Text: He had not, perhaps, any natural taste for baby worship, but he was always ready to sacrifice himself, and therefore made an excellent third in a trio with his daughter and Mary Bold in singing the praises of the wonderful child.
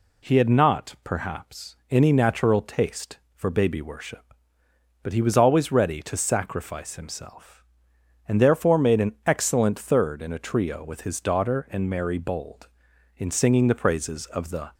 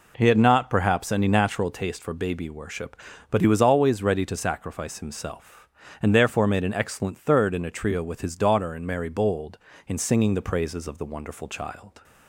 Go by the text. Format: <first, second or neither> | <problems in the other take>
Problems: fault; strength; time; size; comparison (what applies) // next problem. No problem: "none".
second | stops before "wonderful child"; at 14.7 s